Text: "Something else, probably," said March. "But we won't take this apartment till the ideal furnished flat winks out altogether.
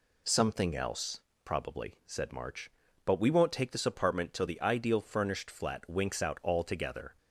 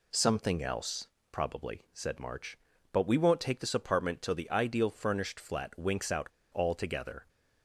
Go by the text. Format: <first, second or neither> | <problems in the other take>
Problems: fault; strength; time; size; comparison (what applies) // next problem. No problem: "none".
first | pauses between "out" and "altogether"; slight; at 6.2 s; 0.27 s long